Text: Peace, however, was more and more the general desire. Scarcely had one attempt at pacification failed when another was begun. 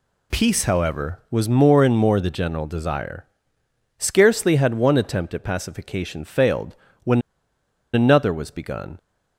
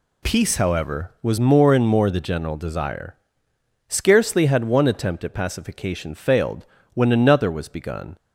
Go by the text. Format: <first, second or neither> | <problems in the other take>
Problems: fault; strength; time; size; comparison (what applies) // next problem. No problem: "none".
second | pauses between "failed" and "when"; slight; at 6.7 s; 0.28 s long; slight in the second // pauses between "when" and "another"; noticeable; at 7.2 s; 0.72 s long